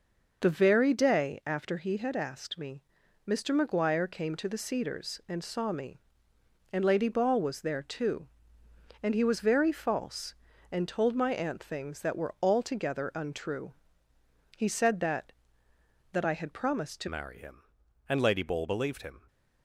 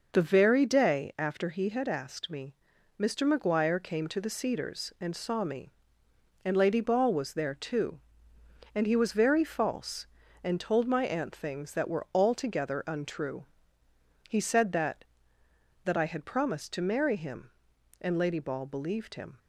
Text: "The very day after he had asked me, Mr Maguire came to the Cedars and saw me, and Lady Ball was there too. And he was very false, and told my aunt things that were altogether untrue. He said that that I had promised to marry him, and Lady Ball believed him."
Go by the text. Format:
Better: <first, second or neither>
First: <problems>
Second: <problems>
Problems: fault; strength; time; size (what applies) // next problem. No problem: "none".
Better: second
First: changes voice at "marry"; from 17.0 s on; 2.2 s long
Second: none